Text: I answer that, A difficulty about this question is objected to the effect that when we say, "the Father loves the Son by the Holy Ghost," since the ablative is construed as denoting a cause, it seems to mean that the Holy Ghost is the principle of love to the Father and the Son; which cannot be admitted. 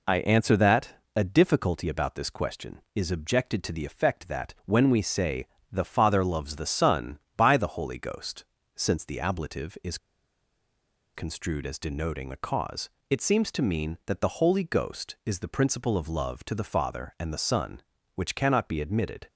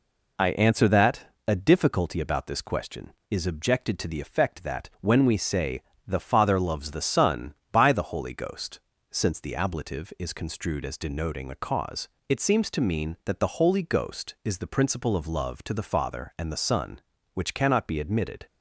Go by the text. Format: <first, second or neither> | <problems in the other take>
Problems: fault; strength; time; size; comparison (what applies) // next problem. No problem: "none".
second | pauses between "is" and "construed"; at 9.9 s; 1.1 s long